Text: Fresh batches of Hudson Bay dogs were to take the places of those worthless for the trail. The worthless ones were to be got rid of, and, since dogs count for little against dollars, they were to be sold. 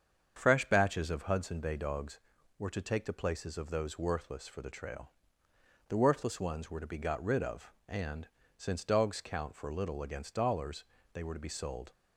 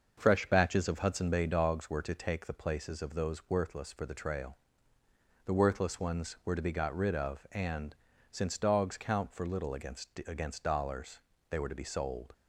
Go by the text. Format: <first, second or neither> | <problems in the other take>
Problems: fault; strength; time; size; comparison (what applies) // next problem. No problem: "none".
first | starts louder than the rest; until 1.1 s; 6 dB; strong in the first // says "against" twice; at 10.2 s